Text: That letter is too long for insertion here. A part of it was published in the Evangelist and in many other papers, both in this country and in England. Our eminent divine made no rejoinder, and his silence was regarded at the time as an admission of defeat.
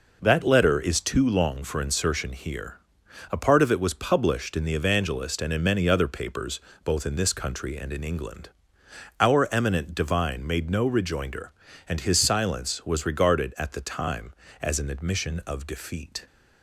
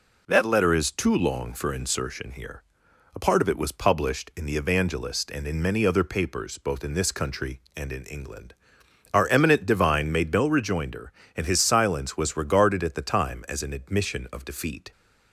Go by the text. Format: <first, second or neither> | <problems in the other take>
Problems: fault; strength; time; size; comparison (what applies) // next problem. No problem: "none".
neither | none